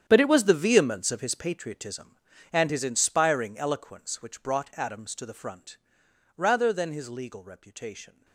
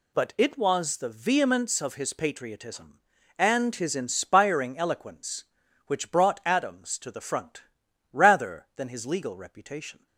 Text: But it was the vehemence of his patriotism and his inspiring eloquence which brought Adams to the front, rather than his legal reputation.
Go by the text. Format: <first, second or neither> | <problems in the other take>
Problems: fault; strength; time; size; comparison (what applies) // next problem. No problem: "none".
second | gets quieter; strong; throughout; 15.5 dB